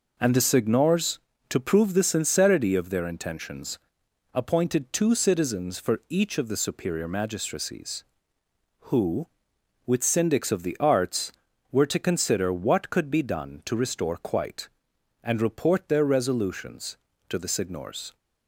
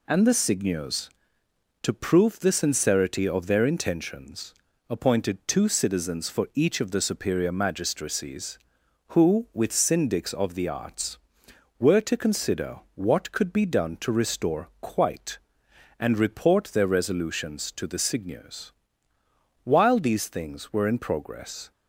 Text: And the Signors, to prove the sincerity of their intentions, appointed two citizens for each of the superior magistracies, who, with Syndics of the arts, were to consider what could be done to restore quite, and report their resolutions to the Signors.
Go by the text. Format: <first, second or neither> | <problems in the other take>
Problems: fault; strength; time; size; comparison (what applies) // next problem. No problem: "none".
first | goes on to say "While these things were in progress"; strong; from 19.6 s on; 2.0 s long